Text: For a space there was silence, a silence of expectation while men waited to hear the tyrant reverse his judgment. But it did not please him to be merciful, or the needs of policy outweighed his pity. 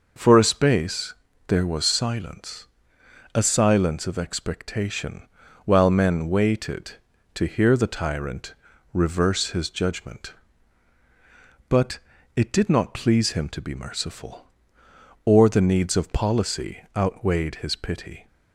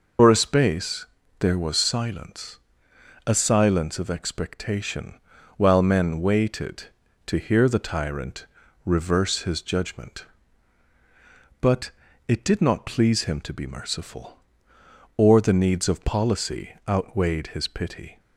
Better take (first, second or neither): first